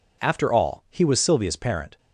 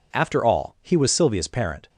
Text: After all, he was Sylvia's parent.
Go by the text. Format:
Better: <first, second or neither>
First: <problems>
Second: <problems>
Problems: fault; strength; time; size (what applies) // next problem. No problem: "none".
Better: neither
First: none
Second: none